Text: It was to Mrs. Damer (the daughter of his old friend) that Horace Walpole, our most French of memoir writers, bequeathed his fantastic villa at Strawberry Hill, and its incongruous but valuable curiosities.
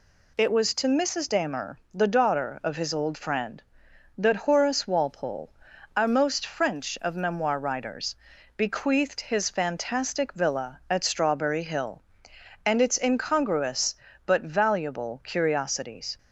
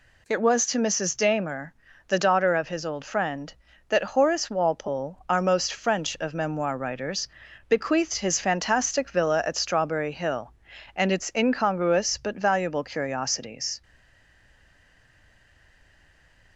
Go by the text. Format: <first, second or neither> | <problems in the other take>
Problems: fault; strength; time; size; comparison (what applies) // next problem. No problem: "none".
first | stays silent after the last word; strong; from 13.8 s on; 2.7 s long